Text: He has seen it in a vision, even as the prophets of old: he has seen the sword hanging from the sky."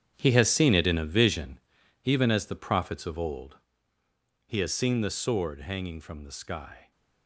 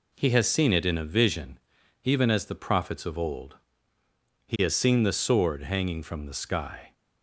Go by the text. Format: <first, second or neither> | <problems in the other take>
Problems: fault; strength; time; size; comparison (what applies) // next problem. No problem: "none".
second | gets quieter; strong; throughout; 12.5 dB